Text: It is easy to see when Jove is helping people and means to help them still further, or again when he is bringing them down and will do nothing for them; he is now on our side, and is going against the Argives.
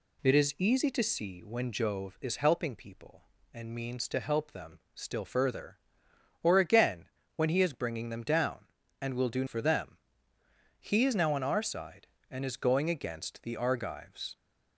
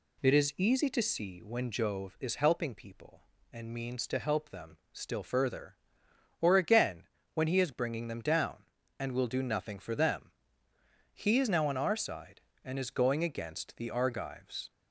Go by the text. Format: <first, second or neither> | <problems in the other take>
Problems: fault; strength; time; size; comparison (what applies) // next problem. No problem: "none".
second | pauses between "them" and "still"; slight; at 4.7 s; 0.16 s long; slight in the second // pauses between "again" and "when"; slight; at 7.0 s; 0.30 s long; slight in the second // skips "nothing"; at 9.4 s